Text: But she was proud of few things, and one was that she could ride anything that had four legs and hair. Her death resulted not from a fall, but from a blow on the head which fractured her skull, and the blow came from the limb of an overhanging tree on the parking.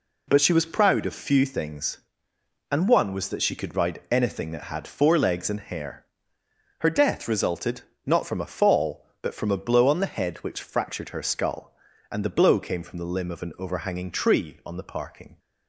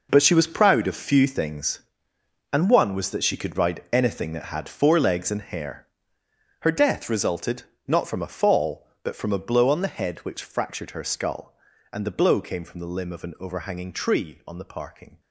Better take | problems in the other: first | gets quieter; strong; throughout; 12.5 dB // pauses between "resulted" and "not"; slight; at 7.6 s; 0.24 s long; slight in the first

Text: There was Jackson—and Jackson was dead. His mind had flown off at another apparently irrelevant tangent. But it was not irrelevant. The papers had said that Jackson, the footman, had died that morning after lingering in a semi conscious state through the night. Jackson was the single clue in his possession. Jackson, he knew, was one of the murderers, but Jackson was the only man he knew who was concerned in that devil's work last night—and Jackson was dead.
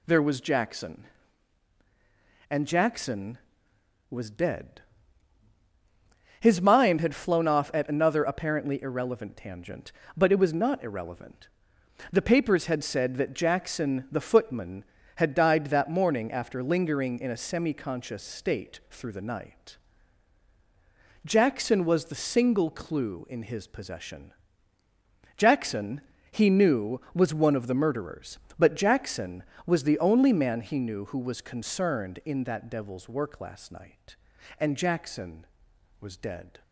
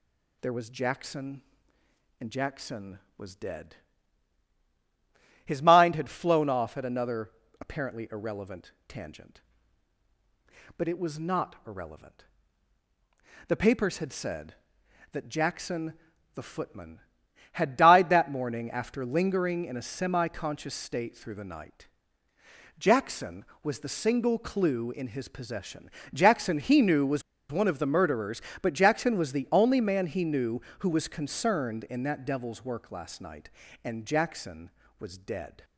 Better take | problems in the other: first | pauses between "another" and "apparently"; slight; at 7.3 s; 0.30 s long // pauses between "was" and "one"; slight; at 27.2 s; 0.30 s long

